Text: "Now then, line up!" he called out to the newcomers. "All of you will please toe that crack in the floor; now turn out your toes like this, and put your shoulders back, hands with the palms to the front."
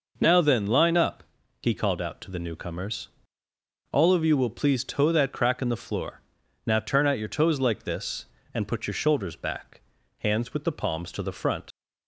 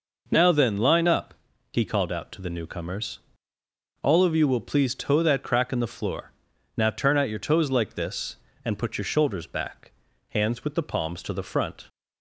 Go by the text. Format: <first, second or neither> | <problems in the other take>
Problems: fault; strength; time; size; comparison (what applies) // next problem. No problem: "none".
second | leaves "front" unfinished; at 11.7 s; 70 ms